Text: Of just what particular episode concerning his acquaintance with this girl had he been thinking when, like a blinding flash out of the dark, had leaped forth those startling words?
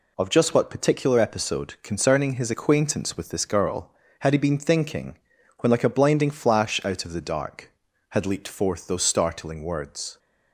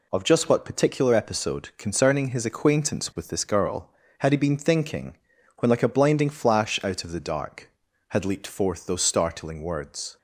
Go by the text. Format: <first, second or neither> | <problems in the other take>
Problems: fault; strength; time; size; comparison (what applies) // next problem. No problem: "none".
neither | pauses between "thinking" and "when"; the same in both